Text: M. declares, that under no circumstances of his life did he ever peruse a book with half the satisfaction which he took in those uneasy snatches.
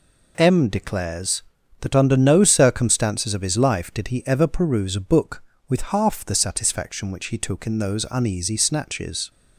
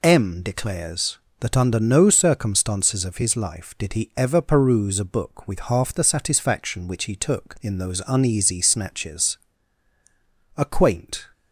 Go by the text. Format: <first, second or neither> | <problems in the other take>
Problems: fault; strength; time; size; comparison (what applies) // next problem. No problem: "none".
first | goes on to say "A quaint"; noticeable; from 10.5 s on; 0.70 s long